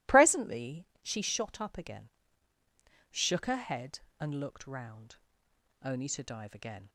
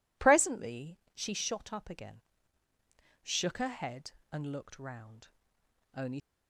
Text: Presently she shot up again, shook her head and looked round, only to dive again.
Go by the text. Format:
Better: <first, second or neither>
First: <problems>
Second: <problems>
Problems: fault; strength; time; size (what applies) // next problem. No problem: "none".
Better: first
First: pauses between "Presently" and "she"; slight; at 0.8 s; 0.16 s long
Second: pauses between "Presently" and "she"; slight; at 0.9 s; 0.16 s long // stops before "to dive again"; at 6.1 s